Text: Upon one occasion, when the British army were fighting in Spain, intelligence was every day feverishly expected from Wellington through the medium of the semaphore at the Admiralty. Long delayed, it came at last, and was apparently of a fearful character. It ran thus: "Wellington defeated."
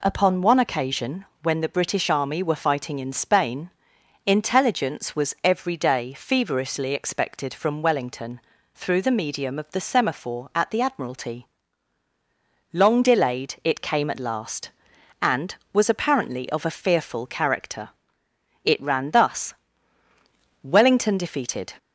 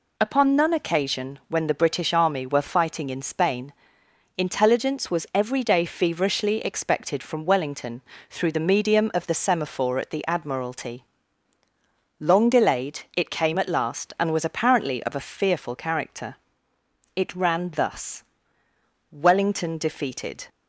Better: first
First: pauses between "Wellington" and "through"; slight; at 8.3 s; 0.36 s long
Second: says "none" for "one"; at 0.5 s // pauses between "Wellington" and "through"; slight; at 8.0 s; 0.30 s long

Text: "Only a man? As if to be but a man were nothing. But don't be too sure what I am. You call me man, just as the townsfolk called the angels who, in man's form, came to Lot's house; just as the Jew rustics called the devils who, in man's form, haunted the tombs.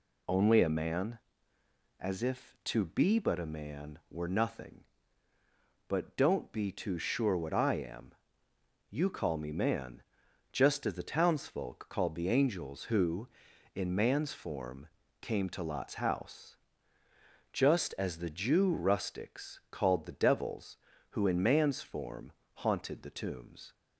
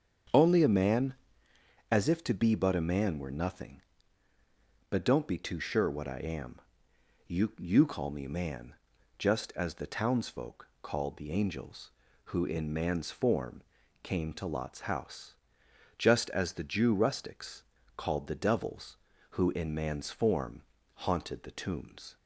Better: first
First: none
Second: starts louder than the rest; strong; until 2.1 s; 7.5 dB // says "You" twice; at 7.5 s // pauses between "rustics" and "called"; slight; at 17.6 s; 0.34 s long

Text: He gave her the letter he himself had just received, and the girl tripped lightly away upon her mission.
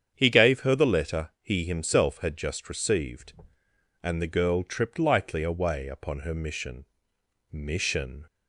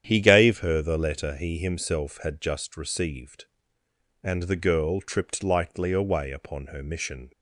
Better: second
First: starts louder than the rest; strong; until 1.1 s; 8.5 dB // says "mission" twice; at 7.5 s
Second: starts louder than the rest; strong; until 1.0 s; 9.5 dB

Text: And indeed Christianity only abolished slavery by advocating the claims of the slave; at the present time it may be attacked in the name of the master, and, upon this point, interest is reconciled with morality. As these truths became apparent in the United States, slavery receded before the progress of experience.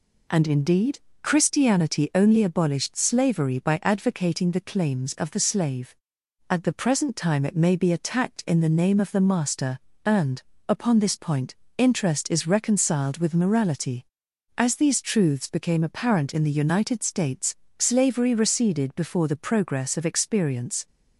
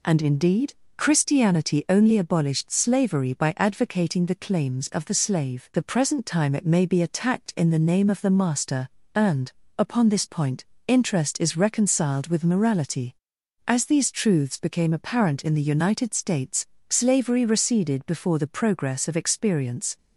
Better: first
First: pauses between "indeed" and "Christianity"; slight; at 0.9 s; 0.22 s long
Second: pauses between "indeed" and "Christianity"; slight; at 0.7 s; 0.22 s long // skips "at"; at 5.7 s

